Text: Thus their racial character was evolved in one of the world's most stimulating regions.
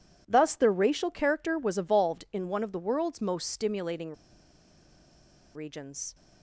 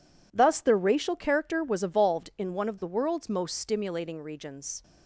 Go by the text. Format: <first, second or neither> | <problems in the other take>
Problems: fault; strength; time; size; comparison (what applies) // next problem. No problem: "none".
second | pauses between "stimulating" and "regions"; strong; at 4.1 s; 1.4 s long